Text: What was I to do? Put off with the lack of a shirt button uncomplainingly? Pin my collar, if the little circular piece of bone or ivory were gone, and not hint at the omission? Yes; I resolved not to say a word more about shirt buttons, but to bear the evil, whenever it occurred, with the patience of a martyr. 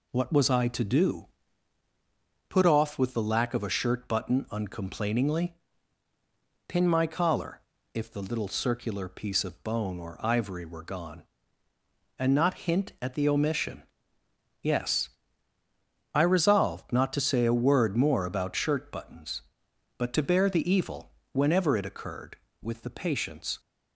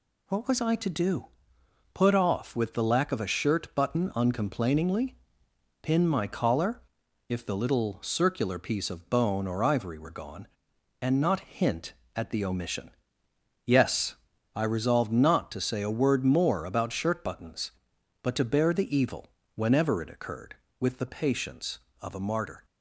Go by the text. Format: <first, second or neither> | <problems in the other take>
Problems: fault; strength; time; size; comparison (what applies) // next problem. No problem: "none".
second | stops before "of a martyr"; at 23.5 s